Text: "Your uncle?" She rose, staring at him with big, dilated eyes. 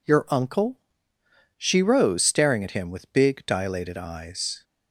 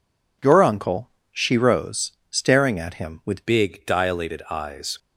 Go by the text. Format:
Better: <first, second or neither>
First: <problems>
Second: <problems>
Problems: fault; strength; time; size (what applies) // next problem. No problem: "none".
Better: first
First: none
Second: changes voice at "big"; from 3.4 s on; 1.5 s long